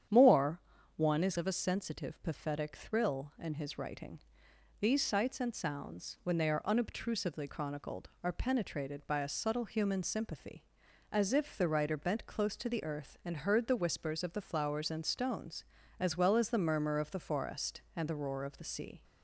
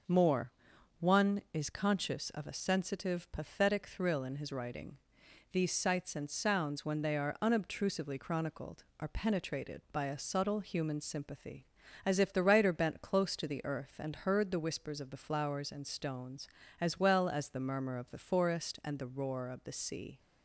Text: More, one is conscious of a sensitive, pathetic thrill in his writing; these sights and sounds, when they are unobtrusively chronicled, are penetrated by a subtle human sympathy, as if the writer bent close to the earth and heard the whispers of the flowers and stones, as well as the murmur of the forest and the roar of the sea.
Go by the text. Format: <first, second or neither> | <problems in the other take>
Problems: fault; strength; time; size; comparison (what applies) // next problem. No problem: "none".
second | starts louder than the rest; strong; until 1.4 s; 9 dB // skips "conscious"; at 1.3 s